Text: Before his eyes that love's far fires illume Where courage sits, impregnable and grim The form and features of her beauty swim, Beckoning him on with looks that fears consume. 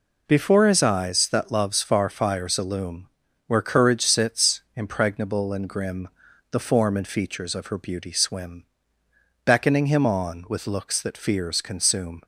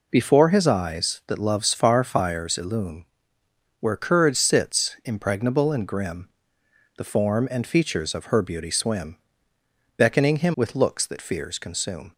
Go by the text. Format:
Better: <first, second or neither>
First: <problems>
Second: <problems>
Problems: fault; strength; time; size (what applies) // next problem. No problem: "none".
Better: first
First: pauses between "illume" and "Where"; at 3.0 s; 0.38 s long // pauses between "grim" and "The"; at 6.0 s; 0.42 s long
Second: pauses between "illume" and "Where"; noticeable; at 3.0 s; 0.74 s long // pauses between "grim" and "The"; noticeable; at 6.2 s; 0.70 s long // skips "on"; at 10.5 s